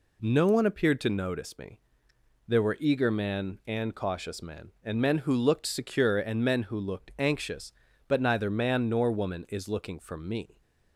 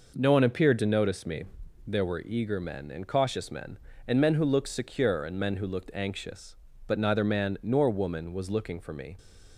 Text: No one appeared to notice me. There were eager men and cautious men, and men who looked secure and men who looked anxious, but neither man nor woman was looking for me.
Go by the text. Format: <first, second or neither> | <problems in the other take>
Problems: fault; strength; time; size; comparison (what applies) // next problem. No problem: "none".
second | says "is" for "was"; at 9.4 s